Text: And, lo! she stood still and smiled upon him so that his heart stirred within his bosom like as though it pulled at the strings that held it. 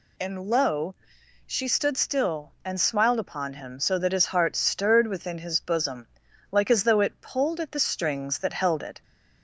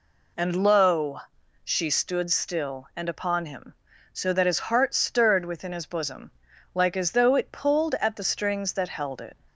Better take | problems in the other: first | skips "smiled"; at 3.0 s // pauses between "bosom" and "like"; at 6.3 s; 0.42 s long; also in the first

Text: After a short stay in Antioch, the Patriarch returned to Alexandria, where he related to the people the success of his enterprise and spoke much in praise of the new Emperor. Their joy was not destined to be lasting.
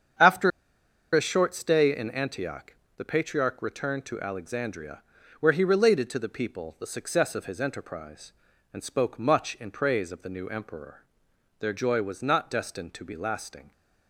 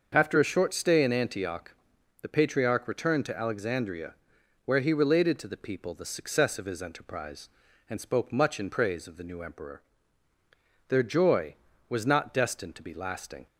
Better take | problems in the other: second | starts louder than the rest; strong; until 1.8 s; 8 dB; also in the second // pauses between "After" and "a"; noticeable; at 0.5 s; 0.62 s long

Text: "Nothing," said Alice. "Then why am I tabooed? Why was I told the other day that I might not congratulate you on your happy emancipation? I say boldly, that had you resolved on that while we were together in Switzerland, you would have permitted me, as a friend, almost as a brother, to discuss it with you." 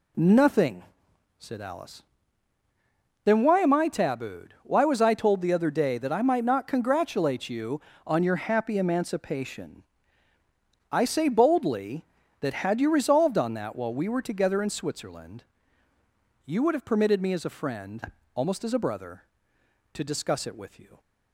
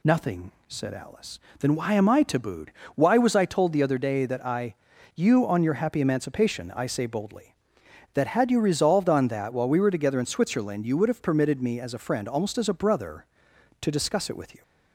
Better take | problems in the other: first | skips "might not congratulate"; at 4.9 s

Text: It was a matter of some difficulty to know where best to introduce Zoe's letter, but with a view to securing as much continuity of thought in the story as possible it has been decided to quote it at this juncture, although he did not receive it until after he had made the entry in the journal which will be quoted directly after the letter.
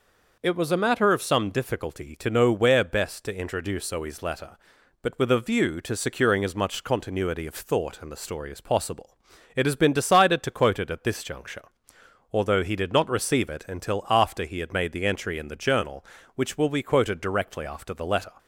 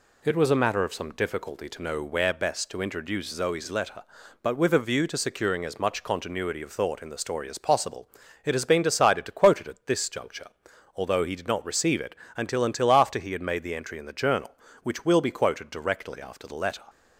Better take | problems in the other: first | pauses between "possible" and "it"; at 8.0 s; 0.38 s long; also in the first // pauses between "it" and "until"; slight; at 12.1 s; 0.22 s long // says "until" twice; at 12.6 s

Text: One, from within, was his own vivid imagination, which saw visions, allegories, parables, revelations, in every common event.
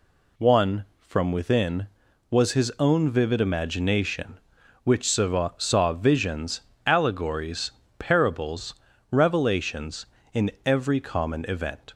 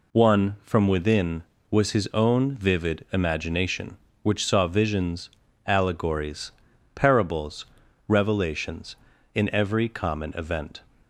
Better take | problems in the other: second | says "saw" twice; at 5.5 s

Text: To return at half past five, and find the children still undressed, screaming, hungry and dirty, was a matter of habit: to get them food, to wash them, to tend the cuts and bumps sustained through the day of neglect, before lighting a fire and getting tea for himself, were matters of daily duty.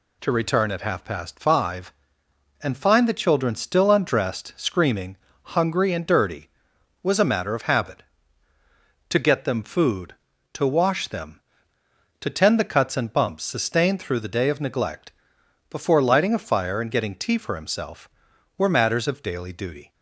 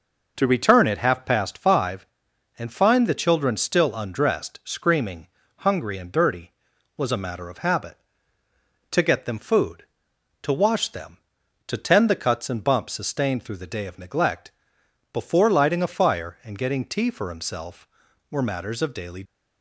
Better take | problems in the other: first | stops before "duty"; at 19.2 s

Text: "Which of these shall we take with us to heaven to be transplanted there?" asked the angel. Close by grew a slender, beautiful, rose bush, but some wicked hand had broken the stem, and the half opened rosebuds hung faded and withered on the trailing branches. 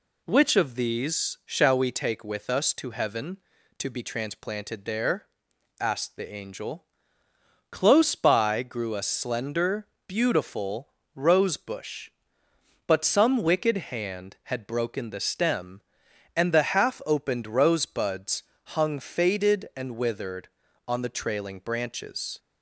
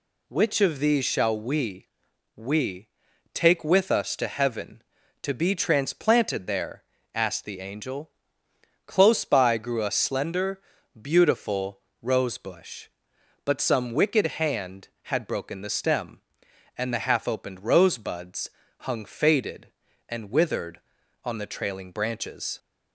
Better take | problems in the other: first | says "we" twice; at 2.3 s // pauses between "rosebuds" and "hung"; slight; at 18.5 s; 0.28 s long; slight in the first

